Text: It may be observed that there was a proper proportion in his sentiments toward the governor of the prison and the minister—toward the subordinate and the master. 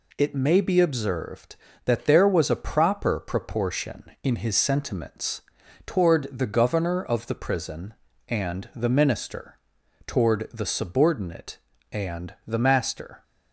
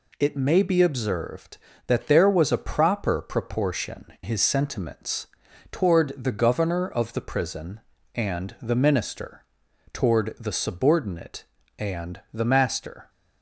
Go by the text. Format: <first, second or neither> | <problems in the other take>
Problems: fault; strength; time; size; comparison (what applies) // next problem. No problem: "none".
first | skips "in"; at 4.1 s // pauses between "sentiments" and "toward"; at 5.2 s; 0.44 s long; also in the first